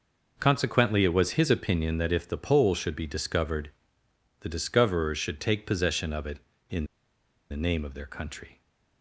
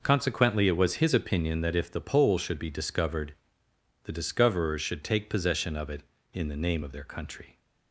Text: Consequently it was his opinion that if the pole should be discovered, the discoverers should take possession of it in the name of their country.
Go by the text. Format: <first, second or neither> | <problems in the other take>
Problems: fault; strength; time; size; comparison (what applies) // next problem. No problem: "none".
second | pauses between "in" and "the"; noticeable; at 6.8 s; 0.65 s long